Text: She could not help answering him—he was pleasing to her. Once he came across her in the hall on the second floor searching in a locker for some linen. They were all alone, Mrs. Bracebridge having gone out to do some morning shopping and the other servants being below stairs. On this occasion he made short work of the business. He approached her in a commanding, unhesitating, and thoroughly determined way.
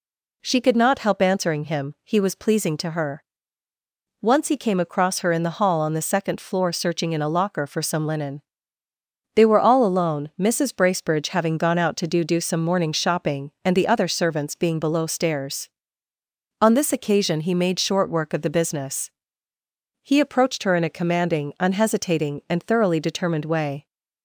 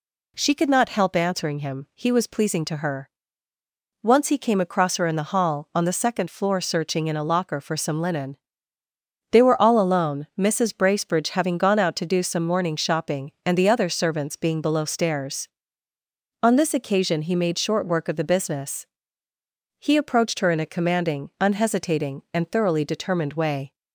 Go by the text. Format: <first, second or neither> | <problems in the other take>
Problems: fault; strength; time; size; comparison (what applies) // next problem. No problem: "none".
second | says "do" twice; at 12.2 s